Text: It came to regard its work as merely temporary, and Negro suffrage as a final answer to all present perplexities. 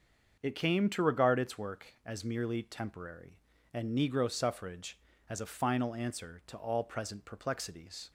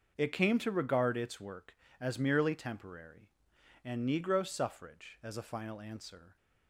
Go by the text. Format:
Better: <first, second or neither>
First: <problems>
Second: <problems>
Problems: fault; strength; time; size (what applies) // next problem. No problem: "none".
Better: first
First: starts louder than the rest; until 1.4 s; 6.5 dB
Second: starts louder than the rest; until 1.1 s; 6.5 dB // stops before "to all present perplexities"; at 6.3 s